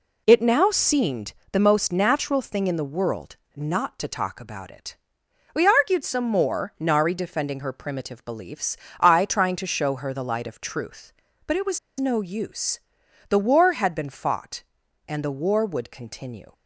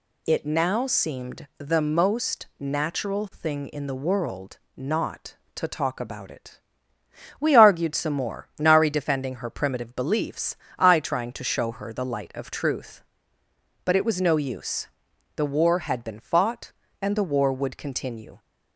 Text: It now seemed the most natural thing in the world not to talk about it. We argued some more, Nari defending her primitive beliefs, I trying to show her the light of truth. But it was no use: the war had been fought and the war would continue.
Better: second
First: pauses between "seemed" and "the"; slight; at 1.3 s; 0.18 s long // pauses between "world" and "not"; slight; at 3.3 s; 0.20 s long // pauses between "was" and "no"; slight; at 11.7 s; 0.20 s long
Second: pauses between "world" and "not"; slight; at 4.5 s; 0.16 s long

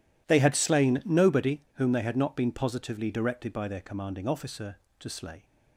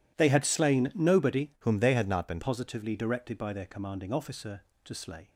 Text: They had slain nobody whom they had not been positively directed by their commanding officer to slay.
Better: first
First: none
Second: changes voice from "whom" to "been"; from 1.5 to 2.3 s; 0.8 s long

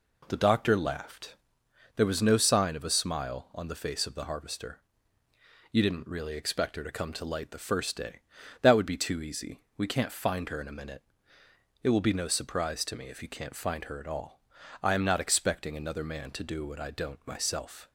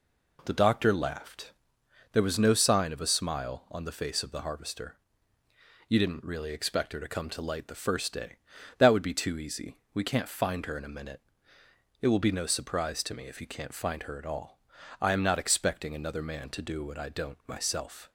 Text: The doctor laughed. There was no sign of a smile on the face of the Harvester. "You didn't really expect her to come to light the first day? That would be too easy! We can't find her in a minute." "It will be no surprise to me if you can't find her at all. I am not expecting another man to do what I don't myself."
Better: neither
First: none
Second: none

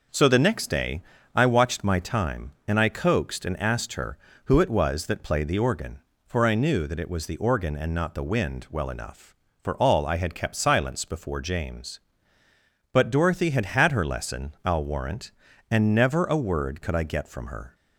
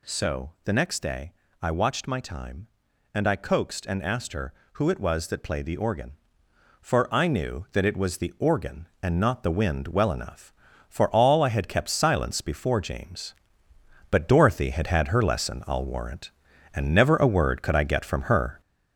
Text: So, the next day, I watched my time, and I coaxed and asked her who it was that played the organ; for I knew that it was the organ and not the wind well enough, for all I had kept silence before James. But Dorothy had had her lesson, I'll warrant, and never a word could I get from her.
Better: first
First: none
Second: gets louder; noticeable; throughout; 4.5 dB

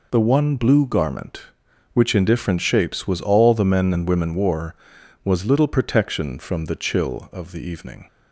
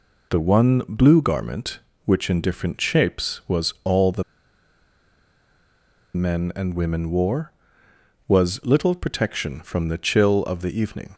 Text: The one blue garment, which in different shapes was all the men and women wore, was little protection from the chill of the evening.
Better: first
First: none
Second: pauses between "the" and "men"; strong; at 4.2 s; 1.9 s long

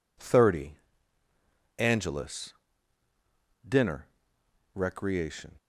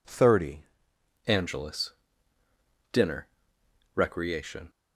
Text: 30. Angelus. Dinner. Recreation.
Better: first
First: none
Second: changes voice at "Angelus"; from 1.2 s on; 3.4 s long

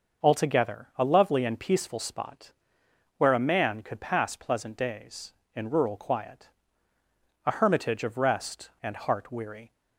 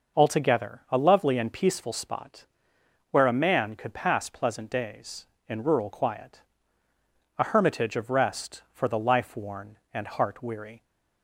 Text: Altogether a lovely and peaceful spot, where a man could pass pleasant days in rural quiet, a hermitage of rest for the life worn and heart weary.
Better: second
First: starts louder than the rest; noticeable; until 1.3 s; 6 dB // skips "for the life worn"; at 8.7 s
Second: none

